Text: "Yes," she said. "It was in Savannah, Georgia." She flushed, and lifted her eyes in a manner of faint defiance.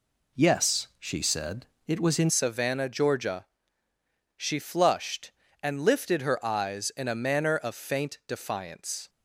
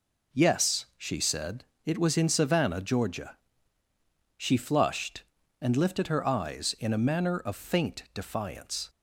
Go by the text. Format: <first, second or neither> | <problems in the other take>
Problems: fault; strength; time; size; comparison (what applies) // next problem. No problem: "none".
second | changes voice at "Savannah"; from 2.2 s on; 6.8 s long